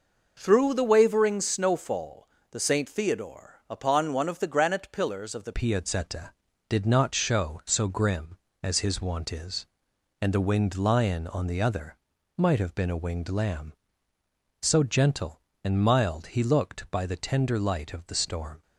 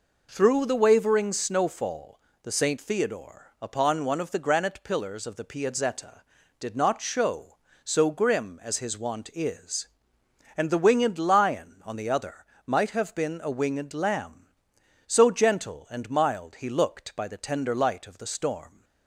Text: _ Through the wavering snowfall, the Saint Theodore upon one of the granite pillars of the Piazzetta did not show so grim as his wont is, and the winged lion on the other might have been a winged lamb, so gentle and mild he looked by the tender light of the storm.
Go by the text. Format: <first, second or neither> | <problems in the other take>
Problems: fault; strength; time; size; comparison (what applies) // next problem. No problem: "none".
second | changes voice at "Piazzetta"; from 5.5 s on; 13.1 s long // pauses between "other" and "might"; at 11.9 s; 0.40 s long; slight in the second